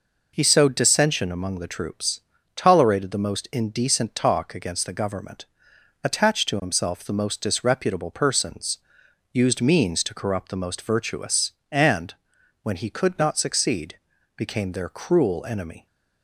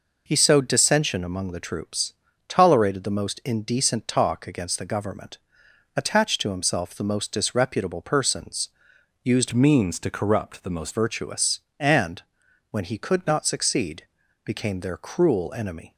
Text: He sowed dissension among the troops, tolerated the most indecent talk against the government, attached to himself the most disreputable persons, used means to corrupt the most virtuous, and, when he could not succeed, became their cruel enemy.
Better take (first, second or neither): first